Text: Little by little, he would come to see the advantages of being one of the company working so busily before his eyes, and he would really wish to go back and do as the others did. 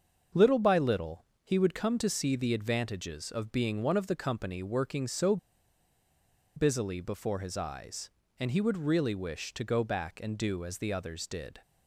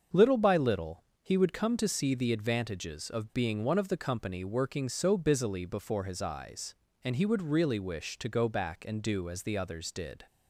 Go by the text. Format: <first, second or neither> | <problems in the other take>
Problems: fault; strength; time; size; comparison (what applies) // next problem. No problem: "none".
second | starts louder than the rest; until 1.5 s; 6.5 dB; also in the second // pauses between "so" and "busily"; at 5.3 s; 1.1 s long